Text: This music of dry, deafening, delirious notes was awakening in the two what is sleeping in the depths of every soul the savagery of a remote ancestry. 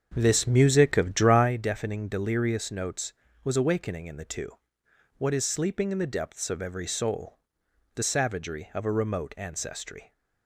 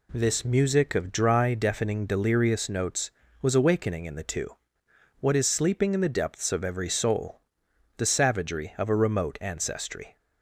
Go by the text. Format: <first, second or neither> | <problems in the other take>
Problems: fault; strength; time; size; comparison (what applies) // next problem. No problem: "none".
second | starts louder than the rest; until 1.5 s; 7 dB // pauses between "two" and "what"; noticeable; at 4.4 s; 0.68 s long; noticeable in the second // pauses between "soul" and "the"; noticeable; at 7.3 s; 0.58 s long; noticeable in the second